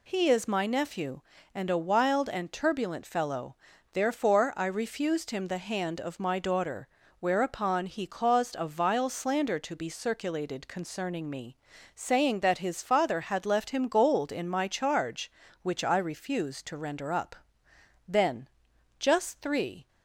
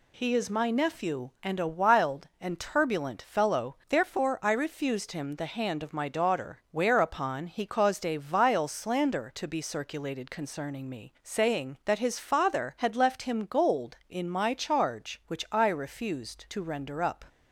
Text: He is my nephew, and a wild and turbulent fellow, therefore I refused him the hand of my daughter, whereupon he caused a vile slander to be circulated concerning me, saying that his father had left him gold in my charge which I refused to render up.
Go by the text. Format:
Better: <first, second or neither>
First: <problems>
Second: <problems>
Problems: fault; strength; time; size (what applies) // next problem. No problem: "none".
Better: second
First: goes on to say "Then just three"; strong; from 18.0 s on; 1.8 s long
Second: none